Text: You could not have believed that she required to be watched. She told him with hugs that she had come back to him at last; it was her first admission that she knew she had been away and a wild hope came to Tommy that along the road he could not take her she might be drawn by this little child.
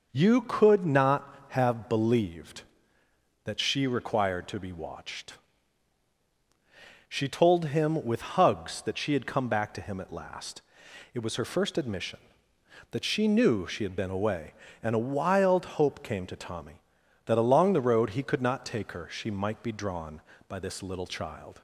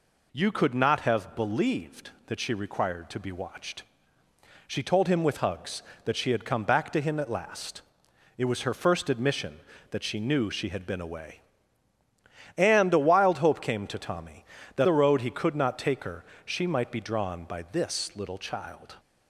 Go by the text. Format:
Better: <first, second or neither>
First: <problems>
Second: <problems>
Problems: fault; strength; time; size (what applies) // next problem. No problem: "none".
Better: first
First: none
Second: skips "along"; at 14.8 s // pauses between "her" and "she"; slight; at 16.2 s; 0.22 s long